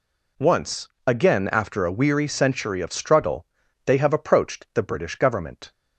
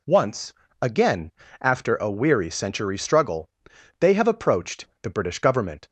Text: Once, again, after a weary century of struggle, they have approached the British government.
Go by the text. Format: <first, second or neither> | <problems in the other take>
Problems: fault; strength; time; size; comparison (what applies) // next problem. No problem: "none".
first | skips "of"; at 2.9 s // pauses between "approached" and "the"; slight; at 4.8 s; 0.16 s long